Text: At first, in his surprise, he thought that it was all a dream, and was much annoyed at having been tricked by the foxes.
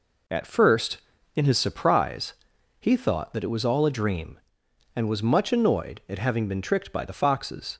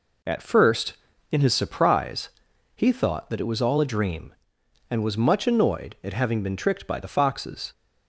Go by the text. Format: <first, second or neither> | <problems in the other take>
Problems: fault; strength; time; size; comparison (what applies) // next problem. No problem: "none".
neither | none